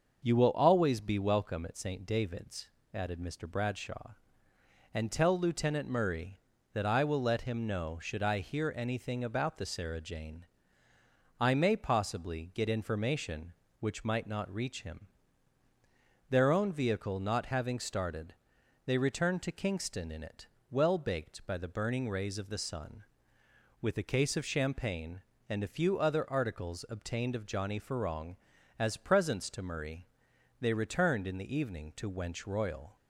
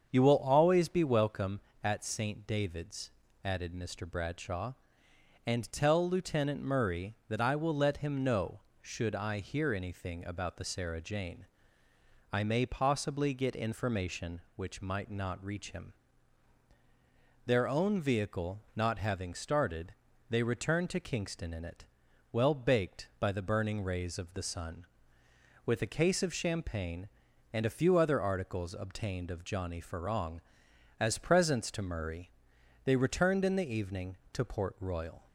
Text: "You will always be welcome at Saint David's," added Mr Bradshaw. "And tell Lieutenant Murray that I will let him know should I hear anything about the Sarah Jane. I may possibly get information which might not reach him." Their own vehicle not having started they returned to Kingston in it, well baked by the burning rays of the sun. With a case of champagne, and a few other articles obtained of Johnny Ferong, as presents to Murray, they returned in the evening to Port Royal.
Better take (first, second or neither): second